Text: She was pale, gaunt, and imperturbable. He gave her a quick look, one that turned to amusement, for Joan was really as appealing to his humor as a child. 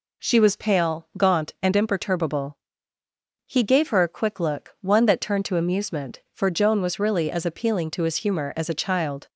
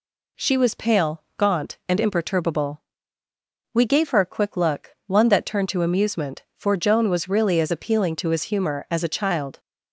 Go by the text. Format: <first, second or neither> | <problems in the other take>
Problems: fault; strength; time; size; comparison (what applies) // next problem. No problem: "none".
first | says "We" for "He"; at 3.7 s